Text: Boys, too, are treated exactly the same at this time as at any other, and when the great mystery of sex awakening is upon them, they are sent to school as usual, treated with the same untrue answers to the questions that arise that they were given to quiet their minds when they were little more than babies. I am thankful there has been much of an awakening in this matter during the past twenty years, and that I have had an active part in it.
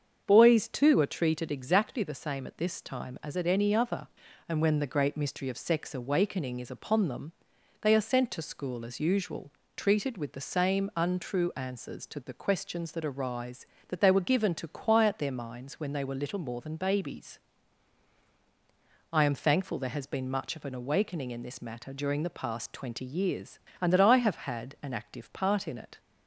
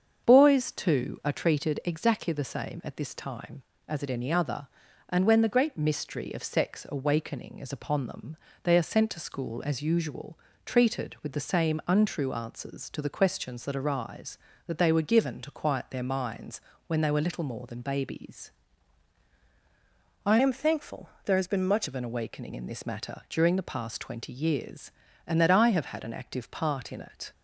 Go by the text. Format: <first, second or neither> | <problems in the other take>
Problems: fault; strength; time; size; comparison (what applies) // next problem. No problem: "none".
first | starts louder than the rest; strong; until 1.3 s; 7 dB; also in the first // pauses between "minds" and "when"; slight; at 16.6 s; 0.26 s long // changes voice from "am" to "much"; from 20.4 to 21.8 s; 1.4 s long // pauses between "thankful" and "there"; slight; at 21.0 s; 0.16 s long